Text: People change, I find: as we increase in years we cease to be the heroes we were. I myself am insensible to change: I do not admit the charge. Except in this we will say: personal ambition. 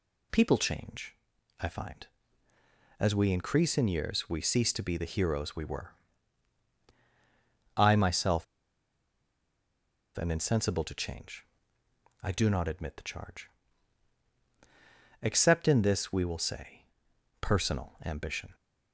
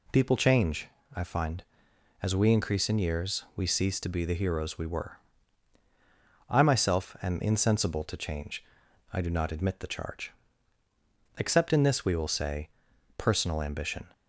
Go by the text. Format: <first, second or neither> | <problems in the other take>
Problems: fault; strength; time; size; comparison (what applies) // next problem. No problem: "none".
second | pauses between "myself" and "am"; strong; at 8.4 s; 1.7 s long